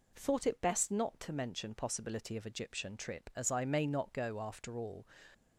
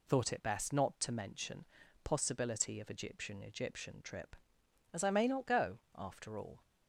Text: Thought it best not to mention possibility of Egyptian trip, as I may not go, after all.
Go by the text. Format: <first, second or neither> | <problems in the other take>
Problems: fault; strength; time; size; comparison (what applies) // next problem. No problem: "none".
first | pauses between "mention" and "possibility"; at 1.6 s; 0.40 s long // says "Egyptian" twice; at 3.4 s